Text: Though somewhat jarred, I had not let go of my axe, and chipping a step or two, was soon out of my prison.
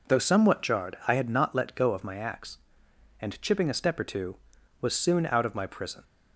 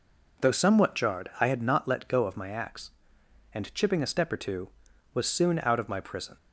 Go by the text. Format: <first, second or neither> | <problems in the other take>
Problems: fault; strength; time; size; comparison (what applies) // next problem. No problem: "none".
neither | none